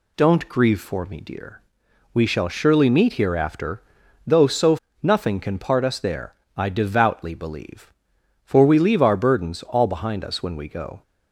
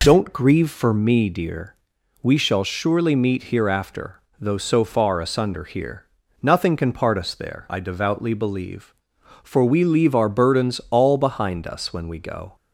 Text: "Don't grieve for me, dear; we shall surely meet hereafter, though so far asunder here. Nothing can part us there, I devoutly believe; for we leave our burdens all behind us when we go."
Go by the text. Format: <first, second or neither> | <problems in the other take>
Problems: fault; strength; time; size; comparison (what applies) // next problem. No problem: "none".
second | skips "far asunder here"; at 4.8 s